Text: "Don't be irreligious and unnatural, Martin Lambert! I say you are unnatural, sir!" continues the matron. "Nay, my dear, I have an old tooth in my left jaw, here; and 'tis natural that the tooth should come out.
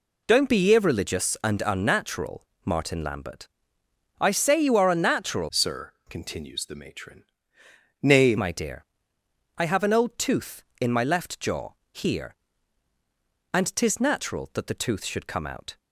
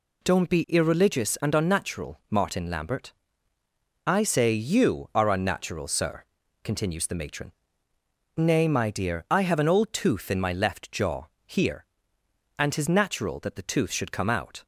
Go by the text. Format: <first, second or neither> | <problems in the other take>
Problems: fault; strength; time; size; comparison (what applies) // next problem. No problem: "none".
second | changes voice from "sir" to "Nay"; from 5.4 to 8.3 s; 2.9 s long